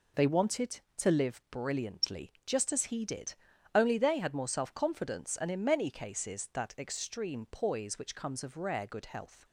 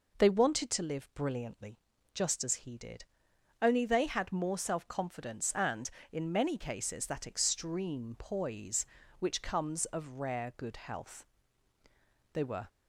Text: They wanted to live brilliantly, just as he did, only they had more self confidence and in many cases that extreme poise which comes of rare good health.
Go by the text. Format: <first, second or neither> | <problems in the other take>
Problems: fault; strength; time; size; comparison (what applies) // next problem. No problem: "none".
first | goes on to say "They were"; slight; from 12.3 s on; 0.34 s long